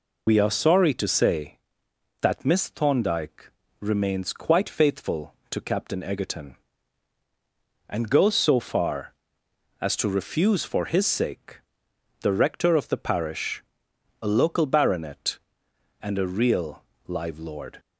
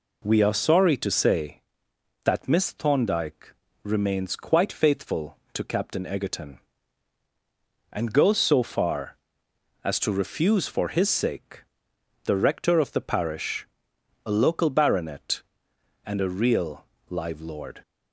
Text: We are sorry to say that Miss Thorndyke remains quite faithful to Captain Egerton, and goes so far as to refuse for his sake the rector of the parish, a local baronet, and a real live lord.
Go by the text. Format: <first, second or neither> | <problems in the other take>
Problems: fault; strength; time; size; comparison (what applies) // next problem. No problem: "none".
second | loses the start of "We"; at 0.2 s; 80 ms // pauses between "Thorndyke" and "remains"; slight; at 3.4 s; 0.30 s long; slight in the second // pauses between "sake" and "the"; noticeable; at 11.6 s; 0.57 s long; noticeable in the second // pauses between "real" and "live"; slight; at 16.8 s; 0.26 s long; slight in the second